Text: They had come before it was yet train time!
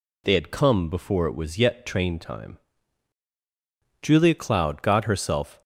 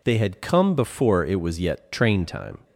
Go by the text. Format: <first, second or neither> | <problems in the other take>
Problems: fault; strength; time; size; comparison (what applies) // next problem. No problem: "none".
second | goes on to say "Julia Cloud got herself"; from 4.0 s on; 1.6 s long